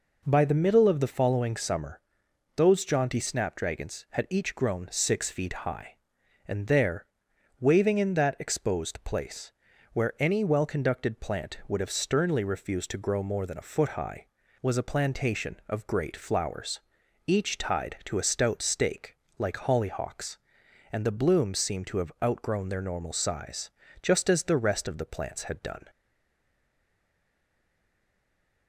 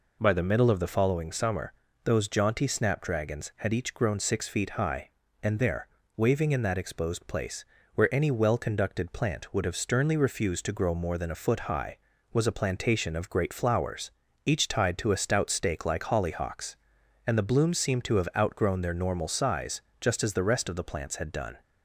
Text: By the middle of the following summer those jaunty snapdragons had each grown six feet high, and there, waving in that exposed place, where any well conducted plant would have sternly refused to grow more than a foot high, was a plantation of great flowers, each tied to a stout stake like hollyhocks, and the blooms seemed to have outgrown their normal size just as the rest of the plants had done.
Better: second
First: pauses between "summer" and "those"; noticeable; at 1.9 s; 0.56 s long // pauses between "stake" and "like"; slight; at 19.1 s; 0.22 s long // pauses between "size" and "just"; slight; at 23.7 s; 0.30 s long // stays silent after the last word; strong; from 25.8 s on; 2.8 s long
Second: pauses between "summer" and "those"; slight; at 1.7 s; 0.32 s long // pauses between "size" and "just"; slight; at 19.8 s; 0.20 s long

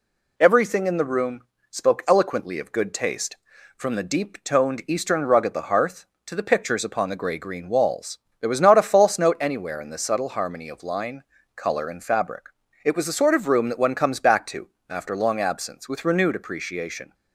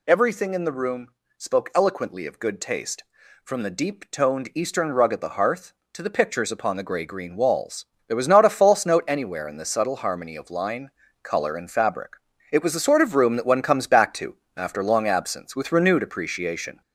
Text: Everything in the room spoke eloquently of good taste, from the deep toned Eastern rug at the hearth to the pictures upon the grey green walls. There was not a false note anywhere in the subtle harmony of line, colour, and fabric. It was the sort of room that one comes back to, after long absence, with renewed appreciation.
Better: first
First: pauses between "room" and "spoke"; slight; at 1.3 s; 0.30 s long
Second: gets louder; noticeable; throughout; 4 dB // pauses between "room" and "spoke"; slight; at 1.0 s; 0.30 s long

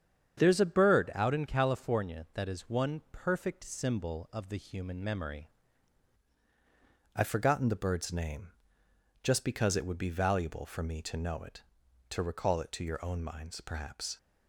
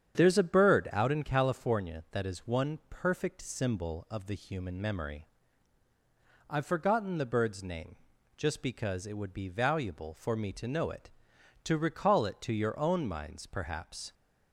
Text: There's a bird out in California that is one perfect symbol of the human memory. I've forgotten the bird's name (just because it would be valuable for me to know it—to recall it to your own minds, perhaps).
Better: second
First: starts louder than the rest; strong; until 1.4 s; 8 dB // changes voice at "I've"; from 7.1 s on; 7.0 s long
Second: starts louder than the rest; strong; until 1.2 s; 8.5 dB

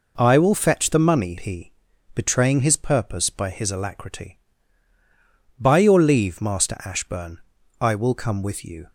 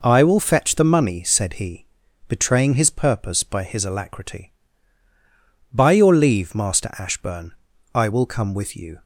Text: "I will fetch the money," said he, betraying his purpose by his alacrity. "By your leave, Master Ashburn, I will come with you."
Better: second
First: skips "said"; at 1.3 s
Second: none

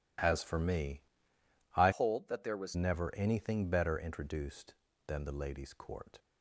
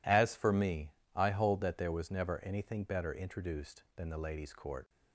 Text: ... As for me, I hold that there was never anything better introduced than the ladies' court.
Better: second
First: changes voice from "hold" to "was"; from 1.9 to 2.7 s; 0.8 s long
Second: none

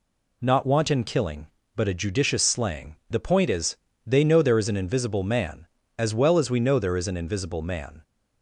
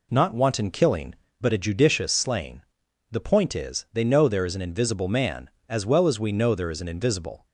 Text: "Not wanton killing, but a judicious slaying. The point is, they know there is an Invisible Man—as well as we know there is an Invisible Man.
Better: first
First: none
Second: stops before "Man"; at 7.4 s

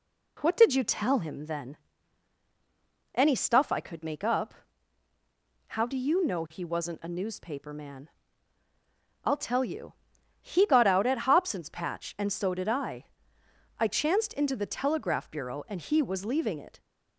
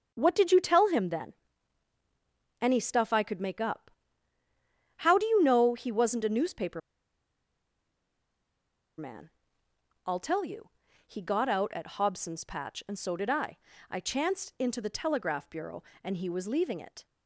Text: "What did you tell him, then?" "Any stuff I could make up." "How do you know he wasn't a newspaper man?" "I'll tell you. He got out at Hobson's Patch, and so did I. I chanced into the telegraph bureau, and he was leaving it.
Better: first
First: none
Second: starts louder than the rest; until 1.1 s; 6.5 dB // pauses between "newspaper" and "man"; strong; at 6.8 s; 2.1 s long

